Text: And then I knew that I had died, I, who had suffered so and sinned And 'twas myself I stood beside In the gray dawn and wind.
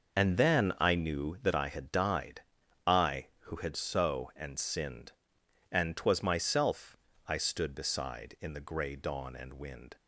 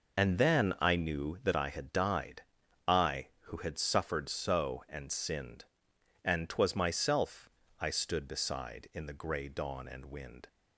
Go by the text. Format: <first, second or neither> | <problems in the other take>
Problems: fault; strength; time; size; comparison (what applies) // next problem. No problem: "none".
second | skips "suffered"; at 3.7 s // pauses between "myself" and "I"; slight; at 6.9 s; 0.32 s long; slight in the second